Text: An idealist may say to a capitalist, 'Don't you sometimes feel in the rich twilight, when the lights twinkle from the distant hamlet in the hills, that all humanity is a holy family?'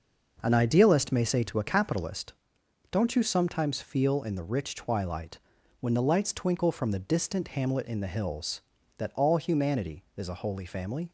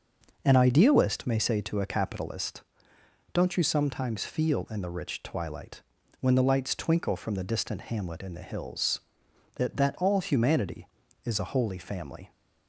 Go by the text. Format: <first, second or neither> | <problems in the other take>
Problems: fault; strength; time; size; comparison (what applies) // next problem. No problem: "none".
first | says "that" twice; at 9.7 s